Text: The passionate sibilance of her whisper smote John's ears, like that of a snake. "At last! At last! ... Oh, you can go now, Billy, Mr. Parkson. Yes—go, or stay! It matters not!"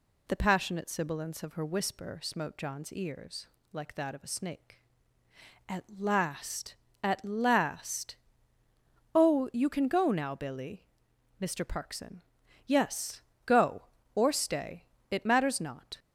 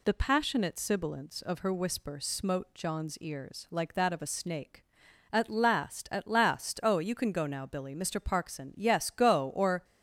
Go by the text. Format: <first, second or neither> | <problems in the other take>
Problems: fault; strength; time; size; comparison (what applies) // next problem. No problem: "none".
first | stops before "stay It matters not"; at 9.8 s